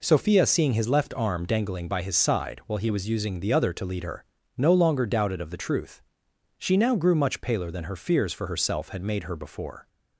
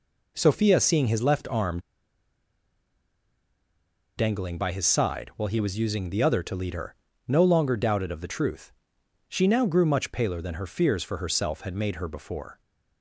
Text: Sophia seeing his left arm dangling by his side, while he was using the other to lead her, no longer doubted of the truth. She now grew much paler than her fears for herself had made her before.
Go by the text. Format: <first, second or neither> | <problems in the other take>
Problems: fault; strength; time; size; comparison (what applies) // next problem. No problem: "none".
first | pauses between "arm" and "dangling"; strong; at 1.7 s; 2.3 s long